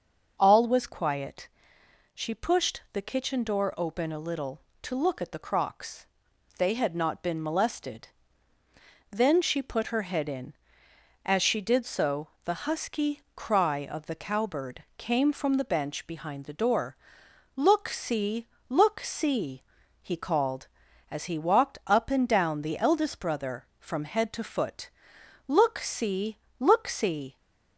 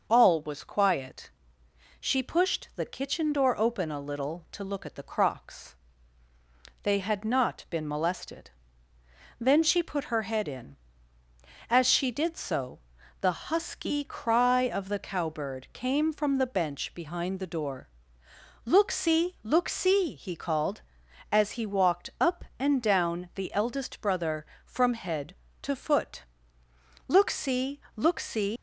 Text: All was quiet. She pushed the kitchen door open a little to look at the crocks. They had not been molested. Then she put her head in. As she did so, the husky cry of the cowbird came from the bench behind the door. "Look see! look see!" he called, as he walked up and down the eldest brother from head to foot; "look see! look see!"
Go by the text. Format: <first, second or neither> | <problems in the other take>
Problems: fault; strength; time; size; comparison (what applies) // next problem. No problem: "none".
first | leaves "see" unfinished; at 28.5 s; 135 ms